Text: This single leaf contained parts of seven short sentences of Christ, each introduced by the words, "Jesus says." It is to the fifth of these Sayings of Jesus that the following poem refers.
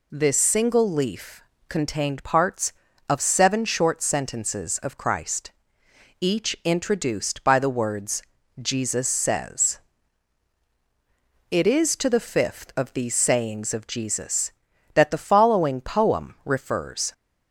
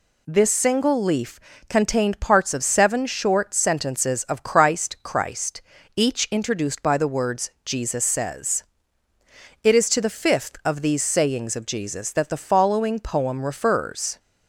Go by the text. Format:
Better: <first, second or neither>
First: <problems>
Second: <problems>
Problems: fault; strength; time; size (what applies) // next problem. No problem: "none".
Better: first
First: pauses between "leaf" and "contained"; slight; at 1.4 s; 0.24 s long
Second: pauses between "leaf" and "contained"; slight; at 1.3 s; 0.32 s long // says "Christ" twice; at 5.0 s